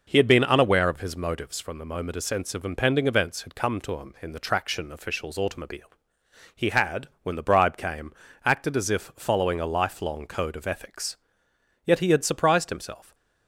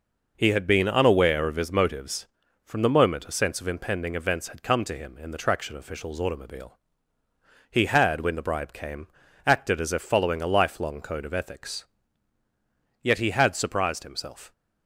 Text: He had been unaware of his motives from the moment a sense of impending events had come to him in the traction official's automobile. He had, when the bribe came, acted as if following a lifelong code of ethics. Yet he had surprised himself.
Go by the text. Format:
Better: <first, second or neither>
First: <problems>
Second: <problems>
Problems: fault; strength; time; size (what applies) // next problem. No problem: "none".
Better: neither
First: none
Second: none